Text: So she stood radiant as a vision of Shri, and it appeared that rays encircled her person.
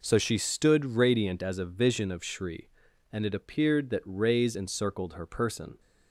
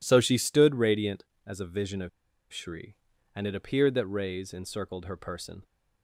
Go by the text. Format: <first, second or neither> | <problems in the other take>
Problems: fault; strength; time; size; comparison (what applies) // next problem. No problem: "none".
first | pauses between "of" and "Shri"; at 2.0 s; 0.43 s long